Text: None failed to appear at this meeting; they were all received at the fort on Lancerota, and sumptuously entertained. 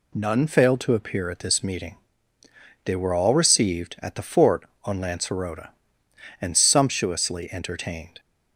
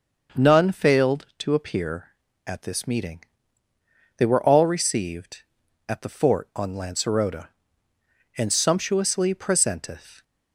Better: first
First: none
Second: starts louder than the rest; noticeable; until 1.4 s; 6 dB // says "presenteth" for "entertained"; at 9.3 s

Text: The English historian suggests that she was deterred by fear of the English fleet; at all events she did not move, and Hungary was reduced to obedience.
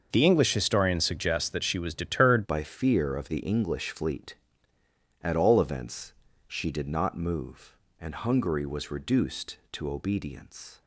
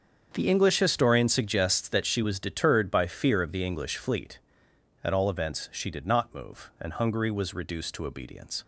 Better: second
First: starts louder than the rest; until 1.1 s; 6.5 dB // changes voice at "by"; from 2.4 s on; 8.4 s long // pauses between "events" and "she"; at 6.1 s; 0.38 s long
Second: starts louder than the rest; strong; until 1.3 s; 7.5 dB

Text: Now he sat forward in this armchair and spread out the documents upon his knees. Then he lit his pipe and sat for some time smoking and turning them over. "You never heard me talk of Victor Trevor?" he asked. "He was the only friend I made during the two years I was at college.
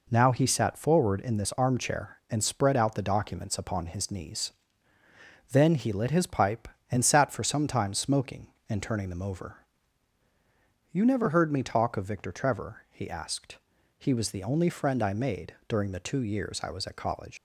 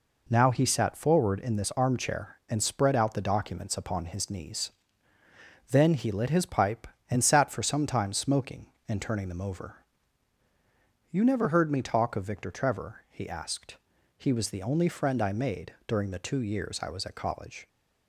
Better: second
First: leaves "college" unfinished; at 17.3 s; 110 ms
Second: none

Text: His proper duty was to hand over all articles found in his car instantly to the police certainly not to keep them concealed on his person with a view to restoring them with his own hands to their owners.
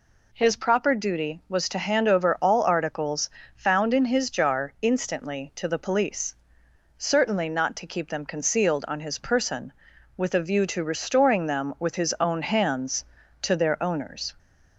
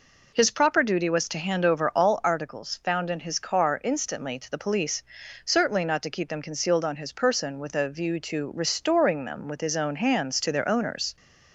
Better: second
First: pauses between "articles" and "found"; slight; at 3.2 s; 0.26 s long // says "jar" for "car"; at 4.2 s // pauses between "police" and "certainly"; noticeable; at 6.3 s; 0.60 s long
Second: pauses between "police" and "certainly"; at 5.0 s; 0.42 s long

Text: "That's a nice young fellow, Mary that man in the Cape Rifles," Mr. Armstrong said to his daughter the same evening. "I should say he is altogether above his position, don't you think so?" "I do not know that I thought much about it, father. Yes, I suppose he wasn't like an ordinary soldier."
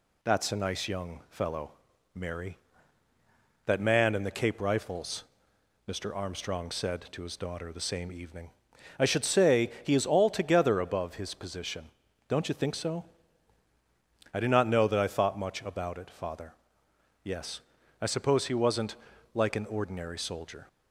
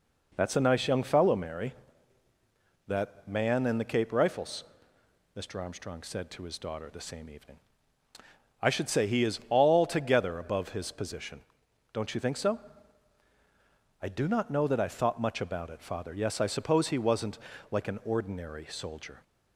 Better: neither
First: pauses between "wasn't" and "like"; at 18.9 s; 0.38 s long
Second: pauses between "wasn't" and "like"; slight; at 17.3 s; 0.32 s long

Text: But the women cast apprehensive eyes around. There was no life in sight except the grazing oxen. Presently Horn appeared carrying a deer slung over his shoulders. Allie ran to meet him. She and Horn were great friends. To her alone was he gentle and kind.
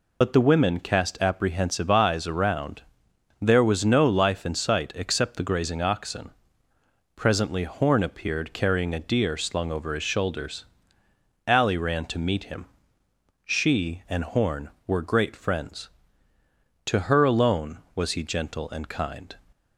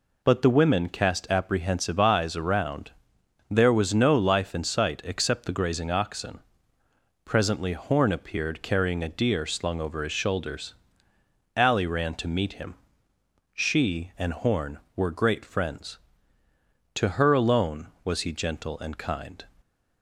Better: second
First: loses the start of "But"; at 0.2 s; 65 ms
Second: none

